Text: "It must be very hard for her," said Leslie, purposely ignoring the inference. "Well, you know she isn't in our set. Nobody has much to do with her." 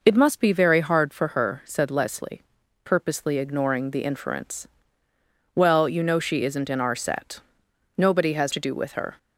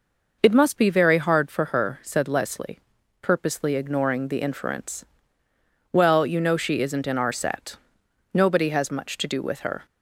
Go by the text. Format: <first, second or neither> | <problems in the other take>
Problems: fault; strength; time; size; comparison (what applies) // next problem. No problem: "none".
second | skips "much"; at 8.5 s